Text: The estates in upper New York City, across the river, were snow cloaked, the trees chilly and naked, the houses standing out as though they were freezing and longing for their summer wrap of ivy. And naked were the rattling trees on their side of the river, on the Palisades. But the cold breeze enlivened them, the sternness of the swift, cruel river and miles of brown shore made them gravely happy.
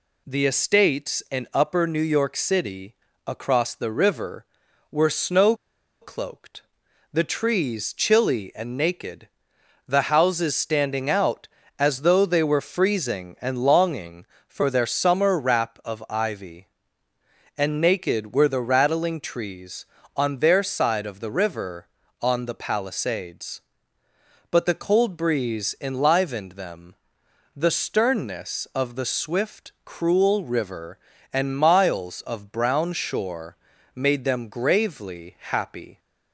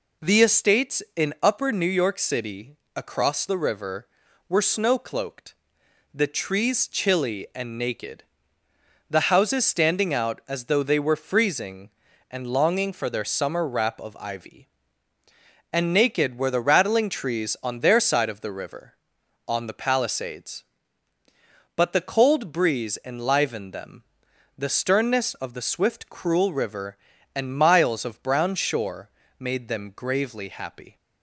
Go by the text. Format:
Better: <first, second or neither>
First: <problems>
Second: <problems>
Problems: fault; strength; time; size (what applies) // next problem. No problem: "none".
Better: second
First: pauses between "snow" and "cloaked"; noticeable; at 5.5 s; 0.47 s long // pauses between "shore" and "made"; at 33.5 s; 0.40 s long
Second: pauses between "shore" and "made"; slight; at 29.0 s; 0.28 s long